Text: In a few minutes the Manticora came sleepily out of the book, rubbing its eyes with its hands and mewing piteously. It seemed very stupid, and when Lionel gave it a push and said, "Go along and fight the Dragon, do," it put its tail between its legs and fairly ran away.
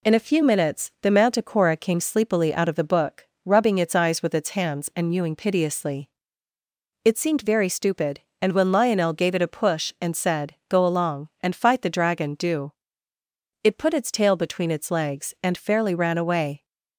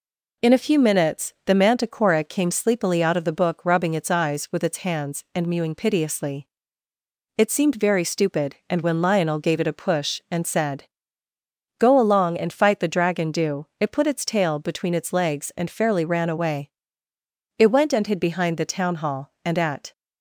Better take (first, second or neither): first